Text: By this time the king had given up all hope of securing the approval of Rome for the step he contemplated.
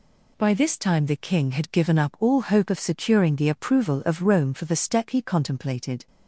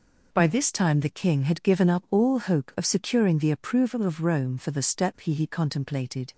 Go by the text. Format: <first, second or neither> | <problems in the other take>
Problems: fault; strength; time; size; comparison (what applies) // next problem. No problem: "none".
first | says "he" twice; at 5.3 s